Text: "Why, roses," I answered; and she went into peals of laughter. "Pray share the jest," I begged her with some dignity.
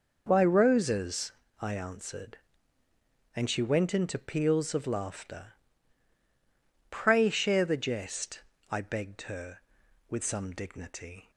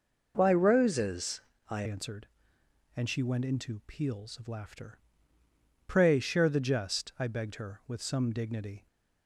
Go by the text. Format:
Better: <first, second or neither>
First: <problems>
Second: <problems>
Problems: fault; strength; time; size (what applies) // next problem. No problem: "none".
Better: first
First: none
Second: changes voice at "answered"; from 1.8 s on; 7.0 s long